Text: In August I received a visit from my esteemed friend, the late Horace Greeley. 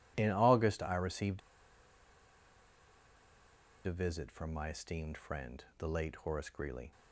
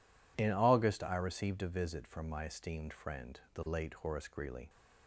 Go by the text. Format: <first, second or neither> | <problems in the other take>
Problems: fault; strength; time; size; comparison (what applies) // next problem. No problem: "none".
second | pauses between "received" and "a"; strong; at 1.3 s; 2.4 s long